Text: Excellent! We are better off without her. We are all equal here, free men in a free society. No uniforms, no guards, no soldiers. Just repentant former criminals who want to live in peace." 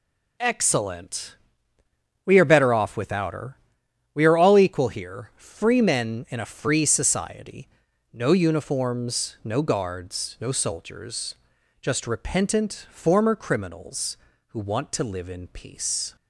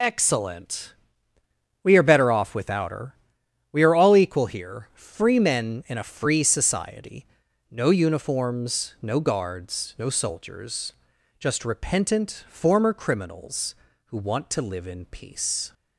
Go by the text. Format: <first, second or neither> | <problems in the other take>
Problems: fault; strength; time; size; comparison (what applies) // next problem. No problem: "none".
first | loses the start of "Excellent"; at 0.0 s; 30 ms